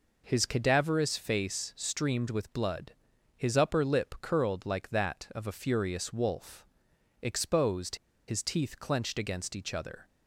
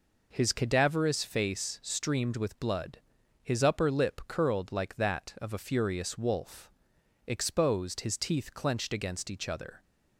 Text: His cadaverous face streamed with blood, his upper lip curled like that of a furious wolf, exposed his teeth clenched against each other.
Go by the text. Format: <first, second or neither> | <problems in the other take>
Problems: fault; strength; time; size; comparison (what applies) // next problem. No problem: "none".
second | pauses between "exposed" and "his"; slight; at 7.9 s; 0.31 s long